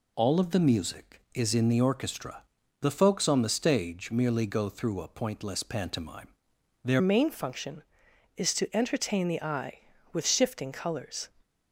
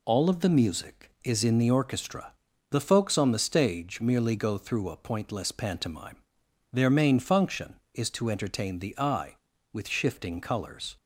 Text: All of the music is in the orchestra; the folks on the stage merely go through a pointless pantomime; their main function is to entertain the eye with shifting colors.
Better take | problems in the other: second | changes voice at "main"; from 6.9 s on; 4.3 s long

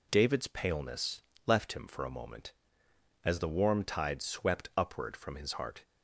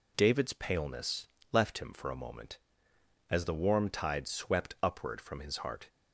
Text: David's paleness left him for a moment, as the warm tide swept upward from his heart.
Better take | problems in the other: neither | pauses between "paleness" and "left"; slight; the same in both

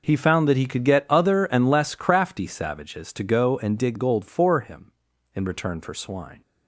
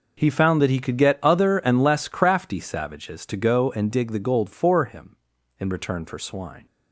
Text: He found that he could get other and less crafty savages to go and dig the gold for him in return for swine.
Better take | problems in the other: second | skips "the"; at 3.9 s

